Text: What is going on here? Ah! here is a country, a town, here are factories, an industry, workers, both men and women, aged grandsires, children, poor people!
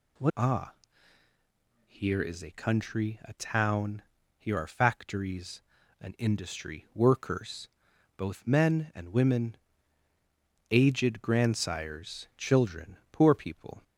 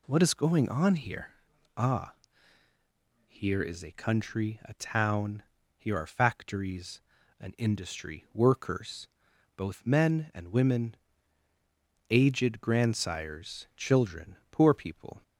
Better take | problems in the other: second | skips "is going on here"; at 0.3 s

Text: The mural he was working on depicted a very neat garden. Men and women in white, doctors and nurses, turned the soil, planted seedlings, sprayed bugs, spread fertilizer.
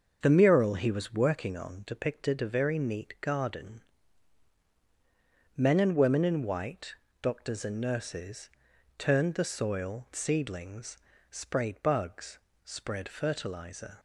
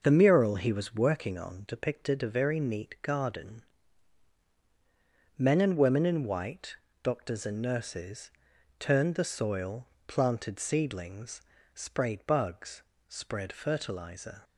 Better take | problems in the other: second | starts louder than the rest; until 1.2 s; 6.5 dB // skips "planted"; at 10.1 s

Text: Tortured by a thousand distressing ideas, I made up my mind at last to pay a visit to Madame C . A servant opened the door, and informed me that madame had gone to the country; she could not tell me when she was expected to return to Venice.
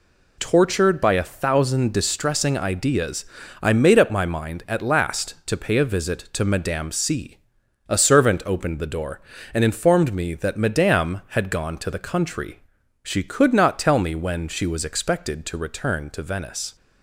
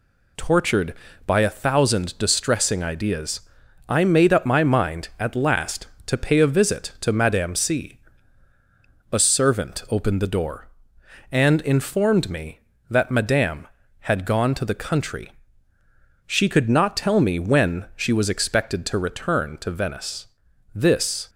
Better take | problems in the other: first | goes on to say "This"; from 20.7 s on; 0.56 s long

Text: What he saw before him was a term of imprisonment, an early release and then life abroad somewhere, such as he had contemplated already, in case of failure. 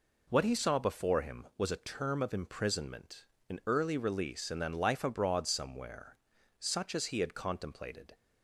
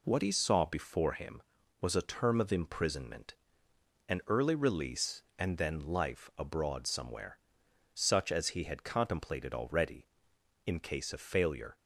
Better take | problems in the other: second | stops before "already in case of failure"; at 8.1 s

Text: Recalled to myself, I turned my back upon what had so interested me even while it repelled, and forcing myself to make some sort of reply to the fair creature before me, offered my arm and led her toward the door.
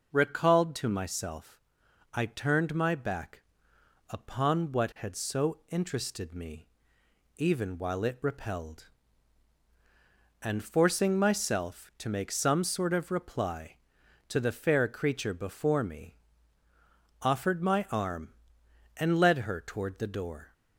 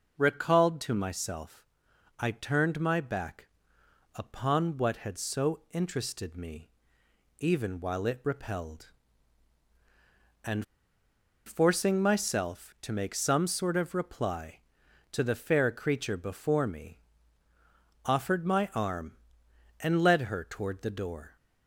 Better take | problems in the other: first | pauses between "back" and "upon"; noticeable; at 3.4 s; 0.68 s long; noticeable in the first // pauses between "me" and "even"; noticeable; at 6.6 s; 0.70 s long; noticeable in the first // pauses between "and" and "forcing"; noticeable; at 10.6 s; 0.81 s long

